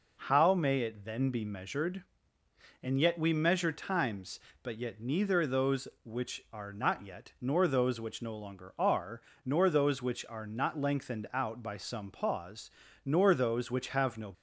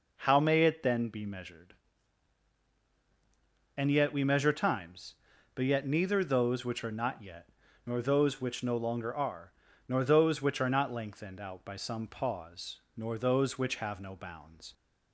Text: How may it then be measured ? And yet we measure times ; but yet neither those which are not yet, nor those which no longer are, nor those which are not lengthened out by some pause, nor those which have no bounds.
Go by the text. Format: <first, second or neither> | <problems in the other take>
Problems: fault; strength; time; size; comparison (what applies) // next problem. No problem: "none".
second | stops before "bounds"; at 14.3 s